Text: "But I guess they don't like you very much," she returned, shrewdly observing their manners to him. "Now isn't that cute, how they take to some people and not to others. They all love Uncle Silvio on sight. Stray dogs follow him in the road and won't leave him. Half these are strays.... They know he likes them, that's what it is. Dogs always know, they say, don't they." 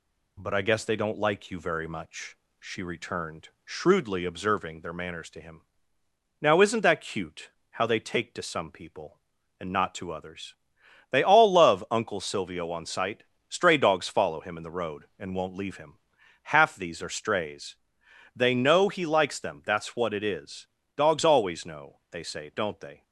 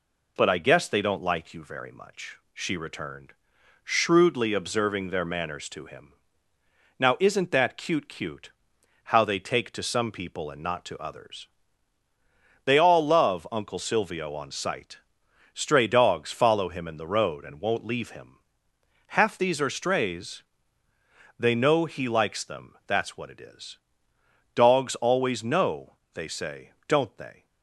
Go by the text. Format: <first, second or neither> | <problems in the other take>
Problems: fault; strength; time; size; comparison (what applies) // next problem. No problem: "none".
first | says "cute" twice; at 8.0 s